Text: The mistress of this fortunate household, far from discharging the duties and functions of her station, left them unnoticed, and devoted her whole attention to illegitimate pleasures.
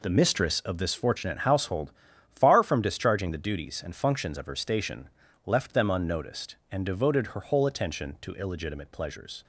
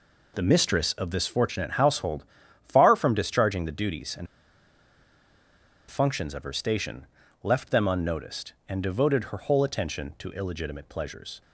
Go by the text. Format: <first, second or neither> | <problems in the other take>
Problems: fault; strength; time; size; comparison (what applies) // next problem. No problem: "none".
first | pauses between "and" and "functions"; strong; at 4.2 s; 1.6 s long